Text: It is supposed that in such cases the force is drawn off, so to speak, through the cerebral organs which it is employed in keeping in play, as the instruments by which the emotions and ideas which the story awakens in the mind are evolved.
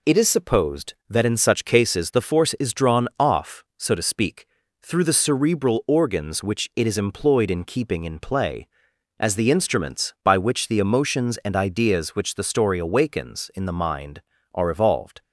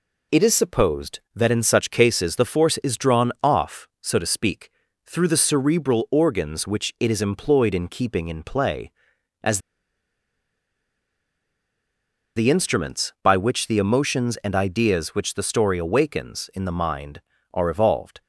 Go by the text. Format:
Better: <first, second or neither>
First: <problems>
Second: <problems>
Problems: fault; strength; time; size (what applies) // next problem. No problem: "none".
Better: first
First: none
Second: pauses between "as" and "the"; strong; at 9.5 s; 2.7 s long